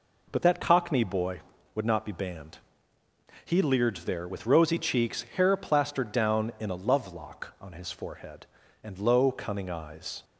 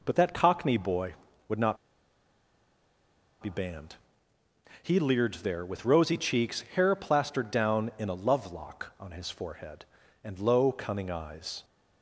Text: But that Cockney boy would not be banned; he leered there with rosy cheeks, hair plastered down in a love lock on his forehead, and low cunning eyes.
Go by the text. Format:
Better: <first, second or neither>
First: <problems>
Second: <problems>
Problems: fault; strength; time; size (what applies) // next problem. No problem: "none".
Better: first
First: none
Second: pauses between "not" and "be"; strong; at 1.7 s; 1.6 s long